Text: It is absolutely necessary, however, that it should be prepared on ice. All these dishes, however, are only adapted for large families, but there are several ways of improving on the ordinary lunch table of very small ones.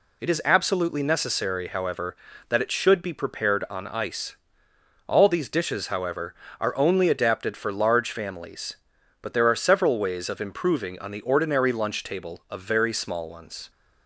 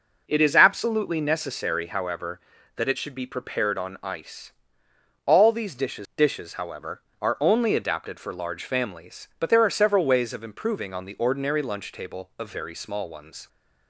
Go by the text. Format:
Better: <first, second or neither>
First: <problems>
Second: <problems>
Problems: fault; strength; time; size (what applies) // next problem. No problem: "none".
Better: first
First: none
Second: says "dishes" twice; at 6.1 s